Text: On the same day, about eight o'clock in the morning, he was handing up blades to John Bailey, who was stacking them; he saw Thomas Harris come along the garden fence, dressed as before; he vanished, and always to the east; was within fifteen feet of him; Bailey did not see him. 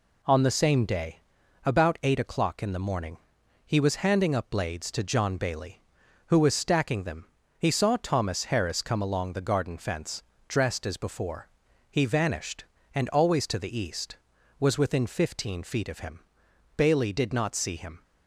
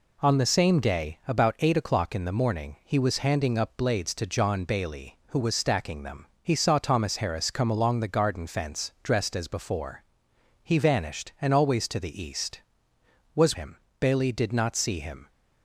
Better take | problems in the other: first | skips "within fifteen feet of"; at 13.5 s

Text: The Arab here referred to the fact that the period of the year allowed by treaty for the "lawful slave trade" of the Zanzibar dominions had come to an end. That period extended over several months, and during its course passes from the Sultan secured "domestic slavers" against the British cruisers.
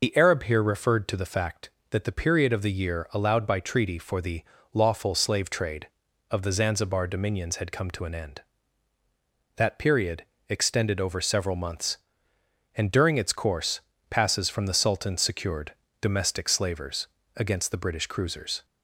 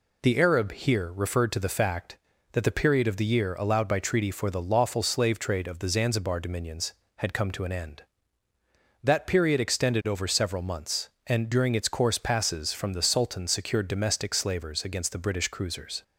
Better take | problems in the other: second | loses the start of "The"; at 0.0 s; 65 ms // pauses between "the" and "lawful"; slight; at 4.4 s; 0.30 s long // pauses between "period" and "extended"; slight; at 10.2 s; 0.24 s long // pauses between "course" and "passes"; slight; at 13.7 s; 0.30 s long // pauses between "secured" and "domestic"; slight; at 15.7 s; 0.28 s long // pauses between "slavers" and "against"; slight; at 17.0 s; 0.30 s long

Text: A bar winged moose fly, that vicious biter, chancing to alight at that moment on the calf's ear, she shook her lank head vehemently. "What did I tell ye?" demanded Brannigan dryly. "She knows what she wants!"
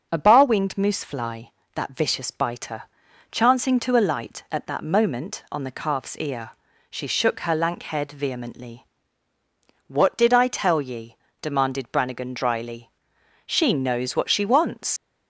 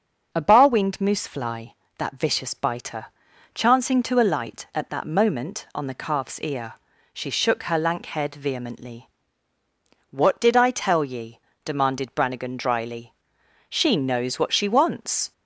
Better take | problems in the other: second | starts louder than the rest; until 1.1 s; 6.5 dB; also in the second // leaves "wants" unfinished; at 14.9 s; 125 ms

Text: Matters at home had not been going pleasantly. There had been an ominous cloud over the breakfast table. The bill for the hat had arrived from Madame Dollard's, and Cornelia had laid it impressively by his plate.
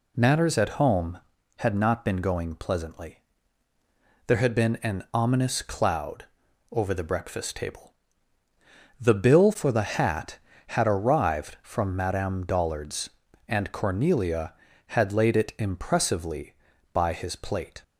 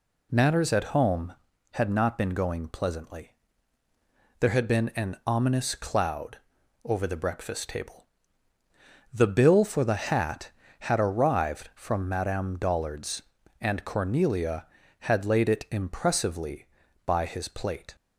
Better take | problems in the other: neither | pauses between "cloud" and "over"; noticeable; the same in both

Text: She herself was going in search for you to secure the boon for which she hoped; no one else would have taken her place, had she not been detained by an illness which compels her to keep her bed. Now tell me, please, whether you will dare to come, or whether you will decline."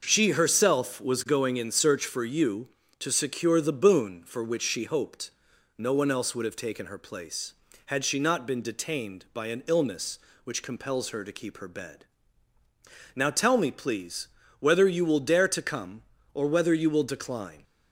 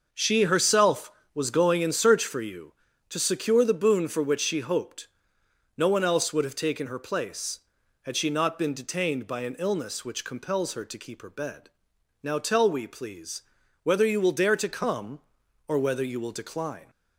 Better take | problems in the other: first | says "we" for "me"; at 12.6 s

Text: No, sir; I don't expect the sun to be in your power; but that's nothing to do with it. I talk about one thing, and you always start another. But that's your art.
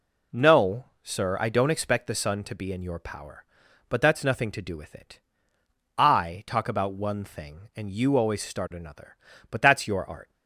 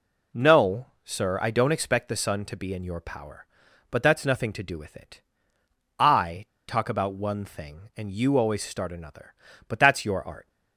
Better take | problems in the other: first | pauses between "I" and "talk"; slight; at 6.4 s; 0.22 s long

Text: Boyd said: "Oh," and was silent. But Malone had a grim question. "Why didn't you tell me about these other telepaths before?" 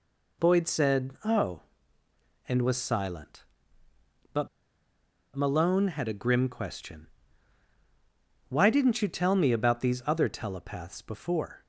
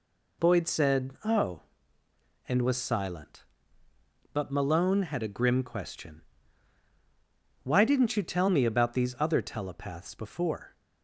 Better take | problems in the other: second | pauses between "But" and "Malone"; noticeable; at 4.4 s; 0.87 s long

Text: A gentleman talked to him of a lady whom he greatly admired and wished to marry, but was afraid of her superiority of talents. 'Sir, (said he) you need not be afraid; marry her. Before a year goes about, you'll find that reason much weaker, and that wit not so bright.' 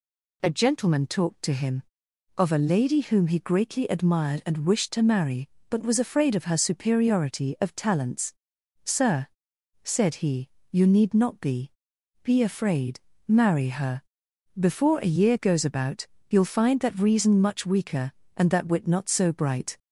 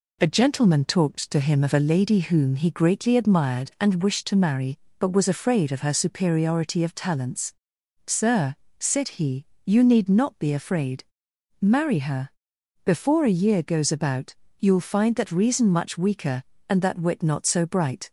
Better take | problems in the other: second | says "be" twice; at 12.2 s

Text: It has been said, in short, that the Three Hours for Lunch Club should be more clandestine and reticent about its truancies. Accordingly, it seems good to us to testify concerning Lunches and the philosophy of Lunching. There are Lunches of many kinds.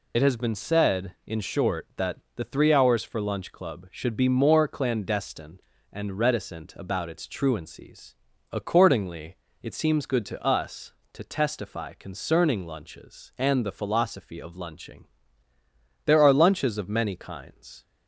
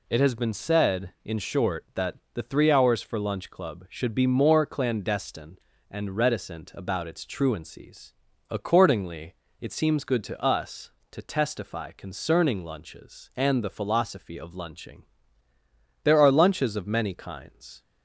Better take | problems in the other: second | loses the start of "It"; at 0.1 s; 50 ms // pauses between "that" and "the"; slight; at 2.1 s; 0.20 s long; slight in the second

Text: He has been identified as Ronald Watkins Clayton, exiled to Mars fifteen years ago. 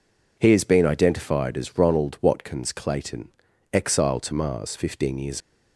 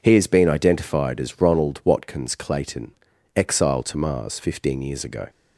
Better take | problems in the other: second | stops before "ago"; at 5.4 s

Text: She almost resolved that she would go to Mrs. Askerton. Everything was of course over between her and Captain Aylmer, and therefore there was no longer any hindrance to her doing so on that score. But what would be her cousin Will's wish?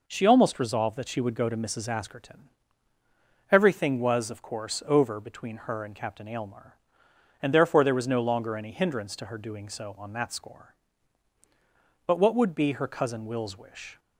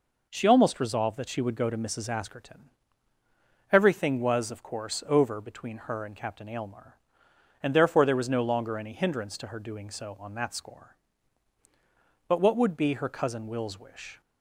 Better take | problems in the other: neither | none

